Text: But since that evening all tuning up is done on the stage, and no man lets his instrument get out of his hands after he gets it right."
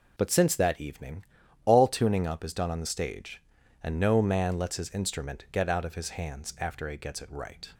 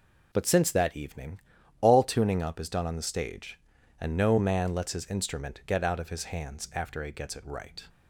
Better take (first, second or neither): neither